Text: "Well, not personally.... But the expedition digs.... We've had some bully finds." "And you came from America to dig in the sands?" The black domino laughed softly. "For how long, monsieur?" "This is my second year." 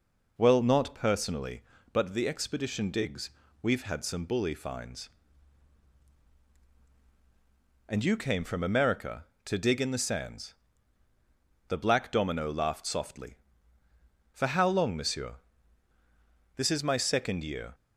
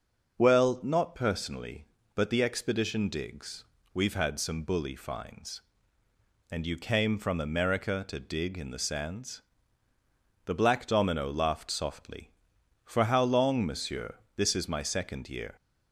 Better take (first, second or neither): neither